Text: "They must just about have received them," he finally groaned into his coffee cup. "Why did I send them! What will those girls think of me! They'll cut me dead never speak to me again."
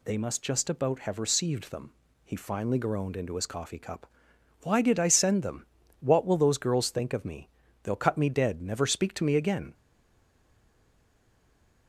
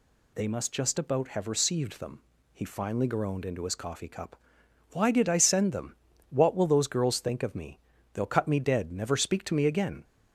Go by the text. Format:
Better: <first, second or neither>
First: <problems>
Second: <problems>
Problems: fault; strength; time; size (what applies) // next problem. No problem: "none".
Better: second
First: stays silent after the last word; from 9.7 s on; 2.1 s long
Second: none